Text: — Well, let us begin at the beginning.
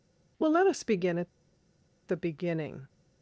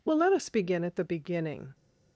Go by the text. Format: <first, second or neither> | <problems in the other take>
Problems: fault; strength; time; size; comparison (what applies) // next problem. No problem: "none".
second | pauses between "at" and "the"; noticeable; at 1.2 s; 0.79 s long